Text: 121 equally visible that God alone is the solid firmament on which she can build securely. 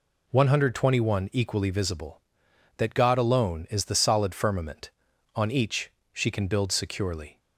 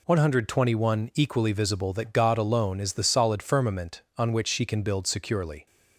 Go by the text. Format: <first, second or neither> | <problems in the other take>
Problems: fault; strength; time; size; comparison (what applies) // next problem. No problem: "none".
second | says "each" for "which"; at 5.4 s